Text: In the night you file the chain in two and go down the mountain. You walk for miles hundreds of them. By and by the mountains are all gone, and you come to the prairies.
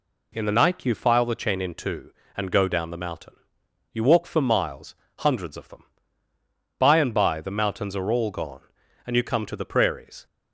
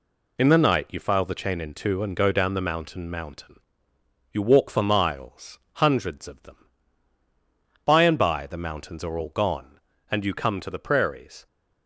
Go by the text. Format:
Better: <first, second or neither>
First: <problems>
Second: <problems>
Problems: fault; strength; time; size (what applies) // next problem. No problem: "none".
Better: first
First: pauses between "miles" and "hundreds"; slight; at 4.9 s; 0.22 s long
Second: says "mountain" twice; at 3.1 s // pauses between "miles" and "hundreds"; slight; at 5.5 s; 0.18 s long